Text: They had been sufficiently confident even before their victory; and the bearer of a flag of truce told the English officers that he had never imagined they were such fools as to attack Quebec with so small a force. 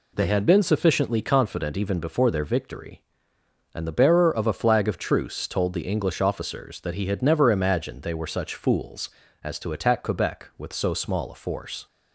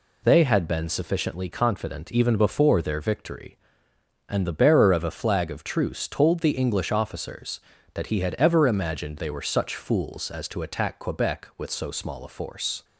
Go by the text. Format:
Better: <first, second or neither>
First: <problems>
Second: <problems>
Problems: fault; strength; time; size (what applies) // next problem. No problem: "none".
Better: first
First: none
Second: says "ever" for "never"; at 8.3 s